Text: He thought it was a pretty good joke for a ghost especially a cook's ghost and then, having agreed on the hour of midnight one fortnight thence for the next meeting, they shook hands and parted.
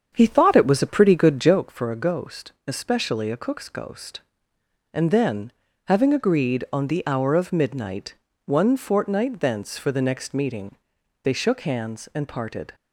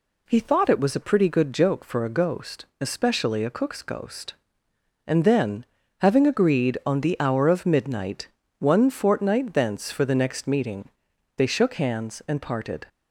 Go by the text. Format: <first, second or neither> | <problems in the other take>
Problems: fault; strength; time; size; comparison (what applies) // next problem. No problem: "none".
second | starts louder than the rest; strong; until 1.7 s; 7.5 dB // pauses between "midnight" and "one"; slight; at 8.1 s; 0.32 s long; slight in the second